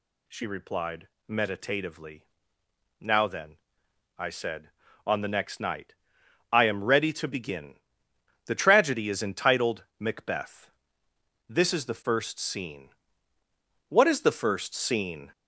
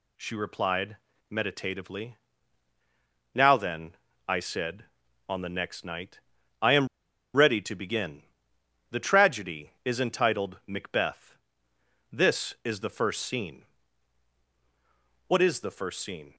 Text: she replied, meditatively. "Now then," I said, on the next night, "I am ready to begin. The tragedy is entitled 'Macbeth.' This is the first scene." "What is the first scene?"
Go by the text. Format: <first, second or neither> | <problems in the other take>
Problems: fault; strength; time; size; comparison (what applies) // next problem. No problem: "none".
first | pauses between "am" and "ready"; noticeable; at 6.8 s; 0.47 s long